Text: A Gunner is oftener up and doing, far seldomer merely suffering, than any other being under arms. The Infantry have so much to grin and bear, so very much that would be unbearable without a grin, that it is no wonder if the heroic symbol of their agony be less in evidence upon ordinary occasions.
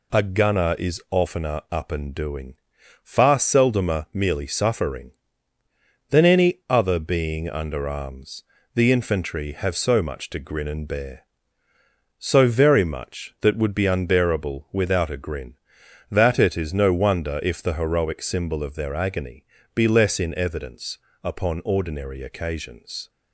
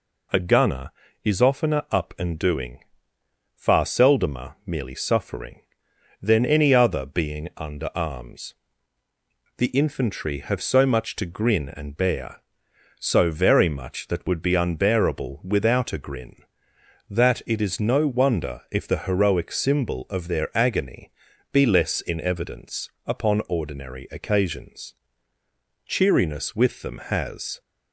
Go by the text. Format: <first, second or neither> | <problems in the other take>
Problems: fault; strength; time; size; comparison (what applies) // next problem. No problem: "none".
first | pauses between "agony" and "be"; at 21.1 s; 0.42 s long; slight in the first // pauses between "evidence" and "upon"; slight; at 22.8 s; 0.16 s long; slight in the first // goes on to say "Cheeriness with them has"; strong; from 25.8 s on; 1.7 s long